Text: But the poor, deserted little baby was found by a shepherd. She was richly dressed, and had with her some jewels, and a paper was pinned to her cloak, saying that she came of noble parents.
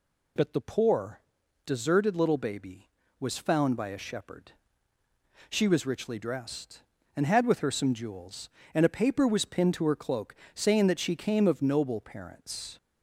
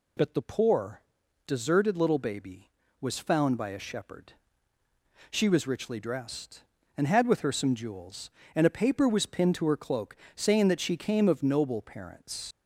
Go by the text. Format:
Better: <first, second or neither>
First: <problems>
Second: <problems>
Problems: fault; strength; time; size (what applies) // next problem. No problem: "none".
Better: first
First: none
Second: leaves "parents" unfinished; at 12.5 s; 70 ms